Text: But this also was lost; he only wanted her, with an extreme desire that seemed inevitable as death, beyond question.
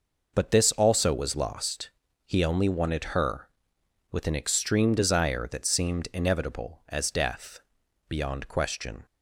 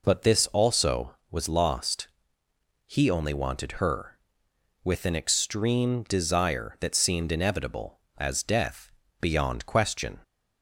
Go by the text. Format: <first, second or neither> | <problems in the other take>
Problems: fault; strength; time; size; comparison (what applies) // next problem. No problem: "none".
neither | none